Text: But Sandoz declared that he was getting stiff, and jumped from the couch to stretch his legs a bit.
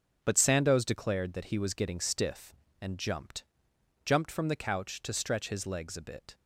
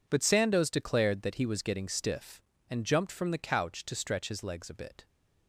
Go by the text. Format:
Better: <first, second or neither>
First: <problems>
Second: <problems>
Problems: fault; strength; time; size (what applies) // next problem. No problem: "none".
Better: second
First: starts louder than the rest; until 1.2 s; 6.5 dB // says "jumped" twice; at 4.0 s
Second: none